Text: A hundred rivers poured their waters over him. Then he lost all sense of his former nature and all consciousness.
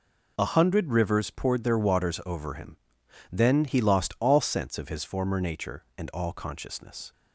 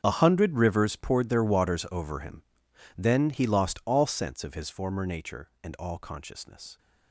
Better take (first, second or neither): first